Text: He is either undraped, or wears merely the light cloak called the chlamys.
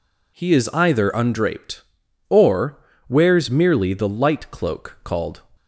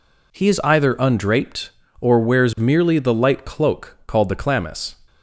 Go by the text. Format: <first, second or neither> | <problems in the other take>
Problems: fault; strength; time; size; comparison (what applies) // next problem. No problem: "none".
second | pauses between "or" and "wears"; slight; at 2.7 s; 0.28 s long // stops before "the chlamys"; at 5.5 s